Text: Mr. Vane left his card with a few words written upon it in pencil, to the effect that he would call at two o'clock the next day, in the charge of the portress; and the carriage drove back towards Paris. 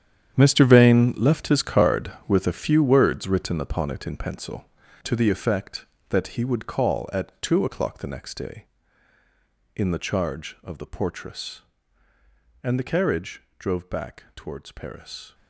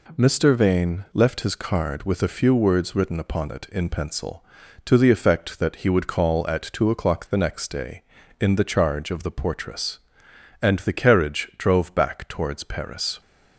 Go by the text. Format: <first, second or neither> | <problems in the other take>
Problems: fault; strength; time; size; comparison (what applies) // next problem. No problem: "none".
second | gets quieter; strong; throughout; 13 dB // pauses between "carriage" and "drove"; slight; at 13.4 s; 0.16 s long